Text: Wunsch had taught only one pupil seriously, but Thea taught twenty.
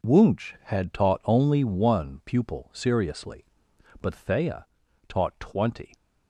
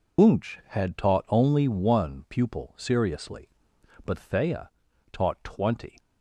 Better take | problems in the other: first | loses the start of "Wunsch"; at 0.1 s; 115 ms // pauses between "Thea" and "taught"; at 4.6 s; 0.44 s long; also in the first

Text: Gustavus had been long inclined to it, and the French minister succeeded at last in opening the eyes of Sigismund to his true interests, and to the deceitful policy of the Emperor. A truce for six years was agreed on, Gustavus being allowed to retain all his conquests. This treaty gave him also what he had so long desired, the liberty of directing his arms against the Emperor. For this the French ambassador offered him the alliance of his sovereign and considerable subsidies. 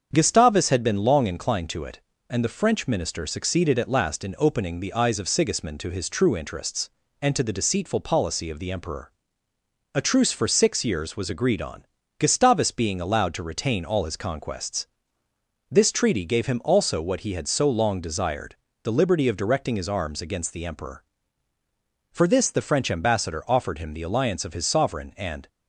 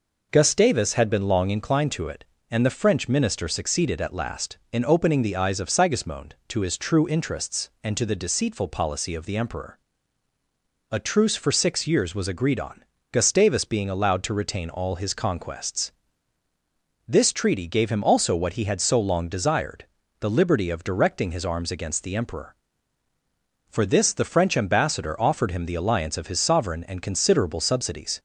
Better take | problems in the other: second | starts louder than the rest; strong; until 1.1 s; 7 dB // stops before "considerable subsidies"; at 25.4 s

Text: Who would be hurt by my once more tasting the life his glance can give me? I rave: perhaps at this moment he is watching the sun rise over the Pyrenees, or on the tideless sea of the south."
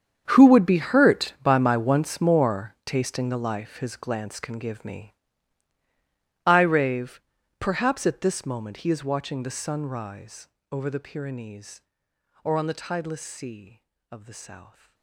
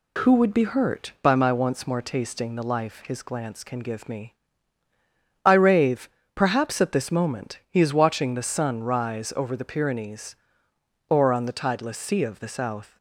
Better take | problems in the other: second | gets quieter; strong; throughout; 17.5 dB // pauses between "rise" and "over"; slight; at 10.4 s; 0.24 s long

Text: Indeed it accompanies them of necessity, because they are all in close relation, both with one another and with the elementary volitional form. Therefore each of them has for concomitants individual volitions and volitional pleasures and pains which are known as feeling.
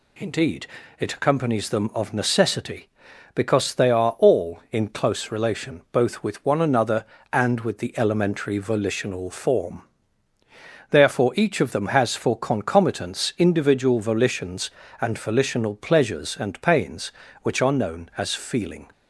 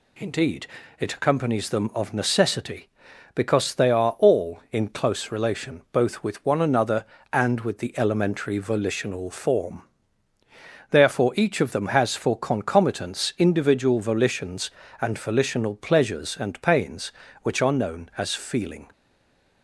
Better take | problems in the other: first | pauses between "Indeed" and "it"; slight; at 0.6 s; 0.32 s long; slight in the first // stays silent after the last word; slight; from 18.9 s on; 0.7 s long

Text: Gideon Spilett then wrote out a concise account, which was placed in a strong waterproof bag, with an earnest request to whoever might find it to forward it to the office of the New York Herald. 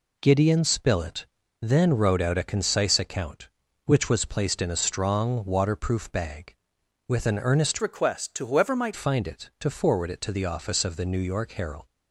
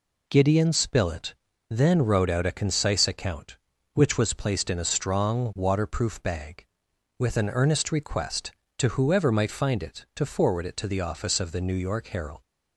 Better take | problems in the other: second | pauses between "Spilett" and "then"; slight; at 1.2 s; 0.36 s long; slight in the second // changes voice from "request" to "might"; from 7.8 to 8.9 s; 1.1 s long

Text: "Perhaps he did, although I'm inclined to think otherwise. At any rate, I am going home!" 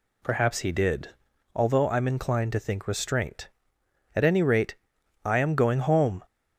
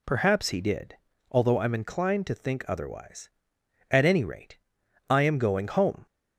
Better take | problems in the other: second | says "restraint" for "otherwise"; at 2.8 s

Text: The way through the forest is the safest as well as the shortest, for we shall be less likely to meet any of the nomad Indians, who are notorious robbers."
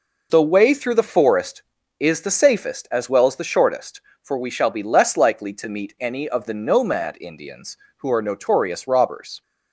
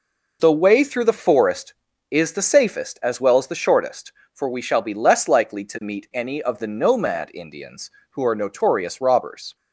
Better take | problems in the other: neither | none

